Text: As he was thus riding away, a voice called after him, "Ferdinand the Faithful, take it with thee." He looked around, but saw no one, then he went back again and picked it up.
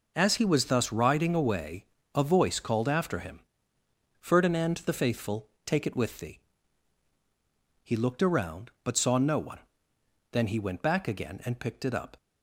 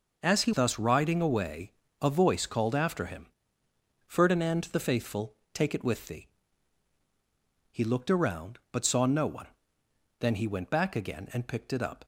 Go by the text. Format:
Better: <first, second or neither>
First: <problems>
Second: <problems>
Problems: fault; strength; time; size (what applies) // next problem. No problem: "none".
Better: first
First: none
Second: skips "was"; at 0.5 s